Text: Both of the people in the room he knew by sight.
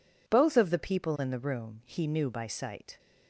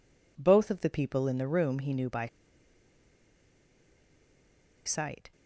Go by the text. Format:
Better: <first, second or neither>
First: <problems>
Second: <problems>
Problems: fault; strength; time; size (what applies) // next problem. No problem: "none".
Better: first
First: none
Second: pauses between "by" and "sight"; strong; at 2.2 s; 2.5 s long